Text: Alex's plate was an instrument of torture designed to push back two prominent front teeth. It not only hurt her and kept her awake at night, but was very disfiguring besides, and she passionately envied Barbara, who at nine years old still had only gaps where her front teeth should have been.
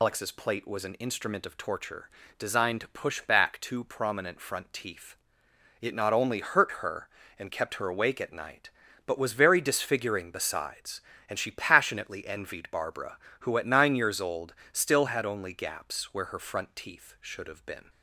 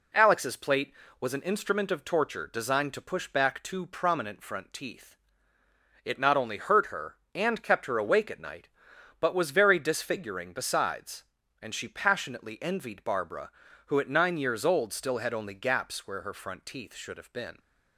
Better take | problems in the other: second | loses the start of "Alex's"; at 0.0 s; 135 ms // pauses between "torture" and "designed"; slight; at 2.0 s; 0.28 s long // pauses between "old" and "still"; slight; at 14.5 s; 0.18 s long

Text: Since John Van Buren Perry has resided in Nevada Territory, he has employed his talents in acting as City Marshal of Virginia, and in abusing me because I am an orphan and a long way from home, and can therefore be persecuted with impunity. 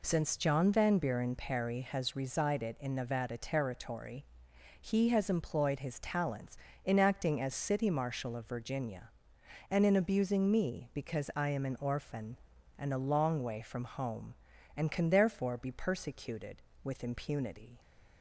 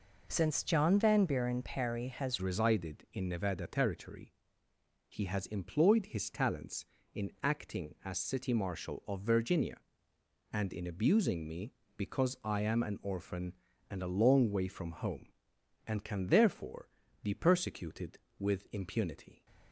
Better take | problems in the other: first | changes voice at "resided"; from 2.4 s on; 17.0 s long // pauses between "therefore" and "be"; slight; at 16.8 s; 0.34 s long

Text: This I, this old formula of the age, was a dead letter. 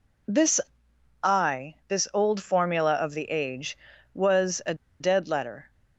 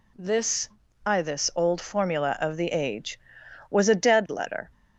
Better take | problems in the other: second | pauses between "This" and "I"; noticeable; at 0.6 s; 0.62 s long; slight in the second // pauses between "a" and "dead"; slight; at 4.7 s; 0.25 s long

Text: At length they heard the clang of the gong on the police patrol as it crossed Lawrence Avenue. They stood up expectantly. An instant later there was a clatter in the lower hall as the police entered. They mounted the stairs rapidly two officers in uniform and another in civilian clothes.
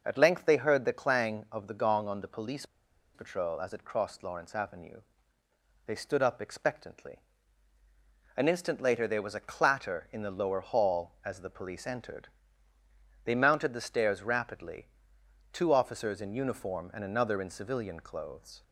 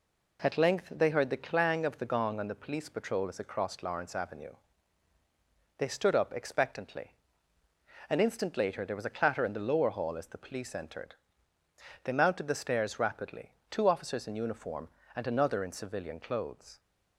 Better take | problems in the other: second | pauses between "police" and "patrol"; noticeable; at 2.6 s; 0.49 s long // pauses between "rapidly" and "two"; noticeable; at 14.8 s; 0.64 s long; slight in the second

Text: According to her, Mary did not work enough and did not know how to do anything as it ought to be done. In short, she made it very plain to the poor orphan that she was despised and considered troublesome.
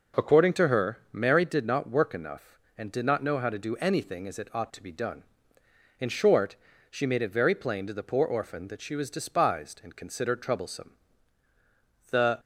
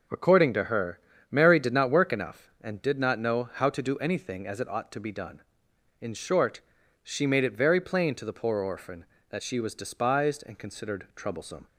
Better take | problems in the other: second | goes on to say "The"; slight; from 12.1 s on; 0.28 s long

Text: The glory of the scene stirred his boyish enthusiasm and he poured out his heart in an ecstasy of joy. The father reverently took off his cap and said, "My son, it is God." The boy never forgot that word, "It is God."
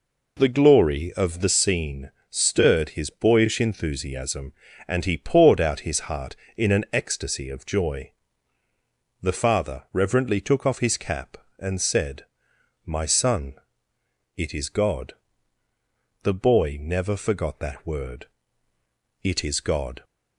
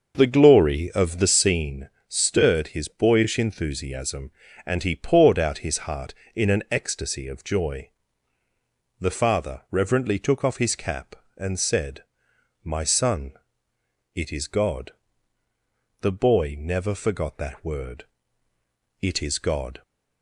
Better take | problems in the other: first | starts louder than the rest; until 1.8 s; 6 dB // pauses between "scene" and "stirred"; slight; at 1.8 s; 0.18 s long; slight in the first

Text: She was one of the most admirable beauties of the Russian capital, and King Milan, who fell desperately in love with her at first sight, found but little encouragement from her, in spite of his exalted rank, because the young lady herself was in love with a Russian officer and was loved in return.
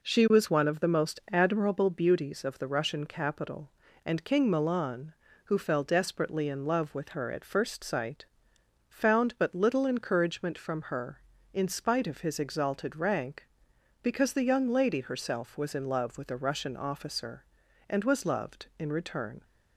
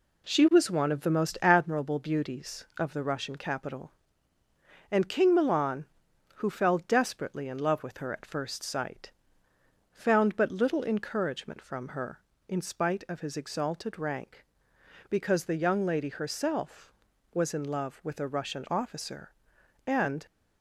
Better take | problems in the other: first | stops before "was loved in return"; at 20.2 s

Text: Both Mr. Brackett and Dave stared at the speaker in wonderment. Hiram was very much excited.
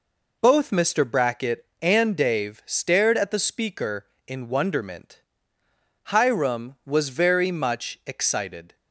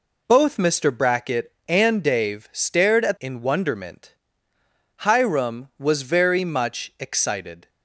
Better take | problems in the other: first | skips "the speaker"; at 3.1 s

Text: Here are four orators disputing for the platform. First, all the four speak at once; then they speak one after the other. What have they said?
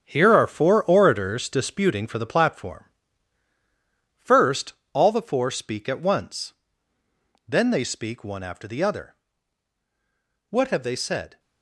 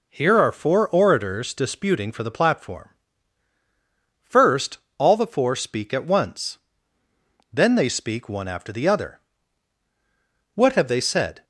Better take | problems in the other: second | gets quieter; strong; throughout; 9.5 dB

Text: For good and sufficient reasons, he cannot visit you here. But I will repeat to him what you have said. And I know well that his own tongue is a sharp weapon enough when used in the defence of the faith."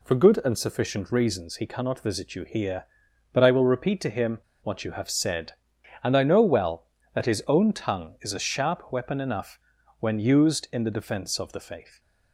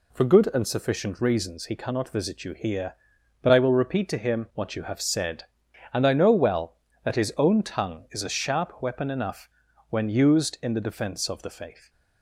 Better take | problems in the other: second | pauses between "him" and "what"; slight; at 4.3 s; 0.22 s long // pauses between "enough" and "when"; at 9.5 s; 0.42 s long; also in the second // stays silent after the last word; slight; from 11.8 s on; 0.5 s long; slight in the second

